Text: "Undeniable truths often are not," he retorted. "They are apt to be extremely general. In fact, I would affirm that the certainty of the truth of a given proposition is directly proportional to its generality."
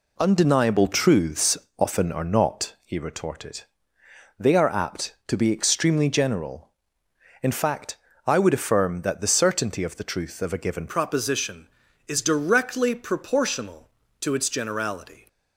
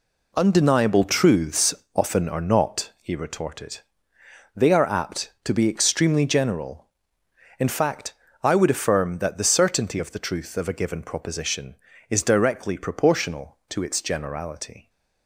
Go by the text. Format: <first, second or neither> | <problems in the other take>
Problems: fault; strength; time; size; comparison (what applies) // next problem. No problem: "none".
second | pauses between "truths" and "often"; slight; at 1.5 s; 0.20 s long; slight in the second // changes voice at "proposition"; from 10.8 s on; 4.4 s long